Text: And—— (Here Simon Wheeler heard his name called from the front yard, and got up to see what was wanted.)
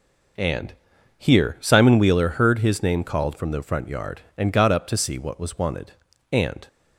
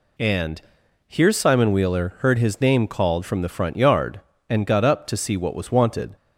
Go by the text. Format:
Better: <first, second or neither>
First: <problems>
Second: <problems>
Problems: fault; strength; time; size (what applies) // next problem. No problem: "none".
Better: second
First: goes on to say "And"; slight; from 6.2 s on; 0.38 s long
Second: none